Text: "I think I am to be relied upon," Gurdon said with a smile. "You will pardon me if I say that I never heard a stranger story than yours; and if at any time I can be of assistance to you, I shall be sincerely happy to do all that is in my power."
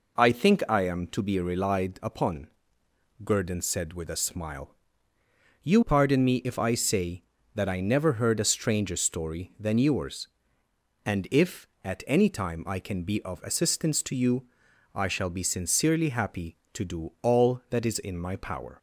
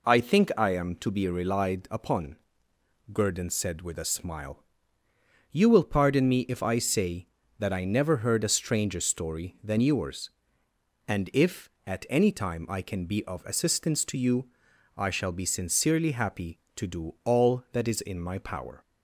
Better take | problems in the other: second | skips "will"; at 5.8 s

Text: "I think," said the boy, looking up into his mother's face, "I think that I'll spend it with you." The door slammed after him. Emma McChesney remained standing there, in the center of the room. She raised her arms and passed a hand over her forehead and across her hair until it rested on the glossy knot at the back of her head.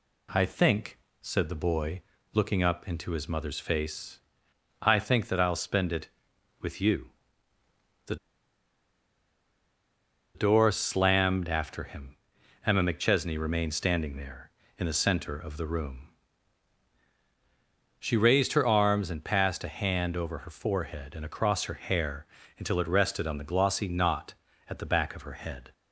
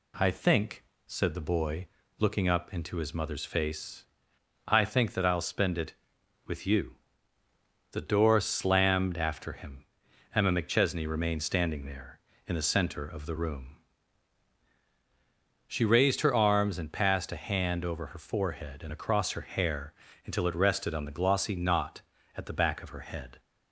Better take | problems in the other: second | pauses between "The" and "door"; strong; at 8.1 s; 2.1 s long // pauses between "hair" and "until"; slight; at 22.2 s; 0.32 s long; slight in the second

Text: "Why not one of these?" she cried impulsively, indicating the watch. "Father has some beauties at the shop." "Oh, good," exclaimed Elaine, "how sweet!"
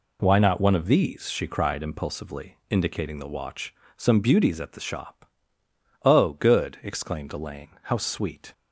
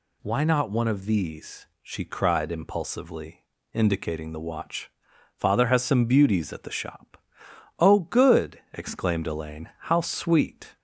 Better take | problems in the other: second | skips "Father has"; at 3.8 s

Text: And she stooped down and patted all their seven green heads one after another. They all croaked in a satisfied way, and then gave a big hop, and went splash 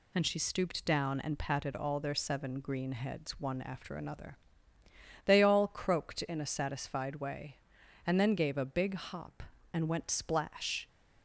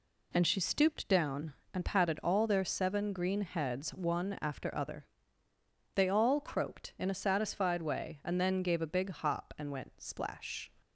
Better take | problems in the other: first | says "other" for "another"; at 4.7 s

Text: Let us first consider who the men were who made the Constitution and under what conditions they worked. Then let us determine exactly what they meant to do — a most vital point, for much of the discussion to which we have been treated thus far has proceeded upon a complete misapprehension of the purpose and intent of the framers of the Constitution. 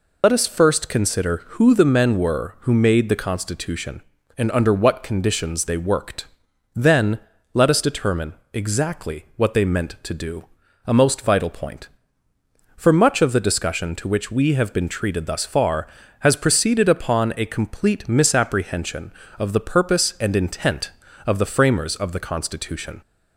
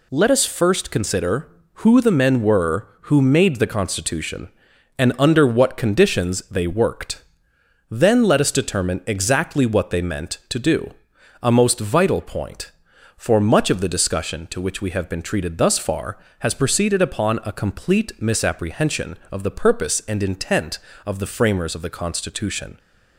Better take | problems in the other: second | loses the start of "Let"; at 0.2 s; 30 ms // pauses between "Then" and "let"; slight; at 7.1 s; 0.34 s long // pauses between "determine" and "exactly"; slight; at 8.3 s; 0.18 s long

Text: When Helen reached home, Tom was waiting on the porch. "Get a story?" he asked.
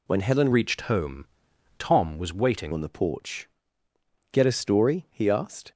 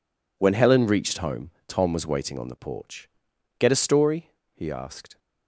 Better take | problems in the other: second | changes voice from "reached" to "waiting"; from 0.5 to 2.7 s; 2.2 s long

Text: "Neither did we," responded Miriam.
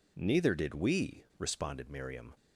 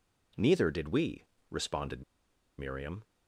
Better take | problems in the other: first | pauses between "responded" and "Miriam"; noticeable; at 2.0 s; 0.57 s long

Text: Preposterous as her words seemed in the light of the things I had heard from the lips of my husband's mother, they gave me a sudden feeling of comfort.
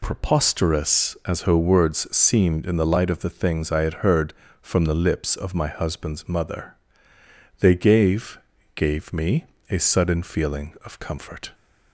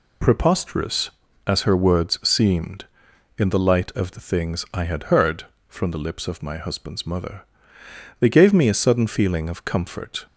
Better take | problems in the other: second | says "gave" twice; at 8.7 s // pauses between "me" and "a"; slight; at 9.4 s; 0.26 s long

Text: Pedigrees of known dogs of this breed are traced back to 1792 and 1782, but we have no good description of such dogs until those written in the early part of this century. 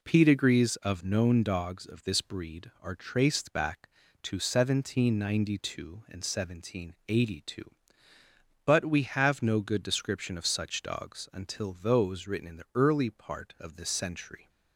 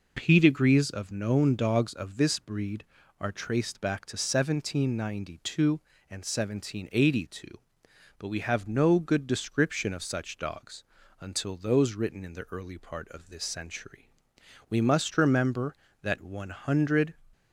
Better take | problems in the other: first | pauses between "dogs" and "until"; slight; at 10.8 s; 0.36 s long // goes on to say "We must remember that one hundred"; strong; from 14.6 s on; 2.4 s long

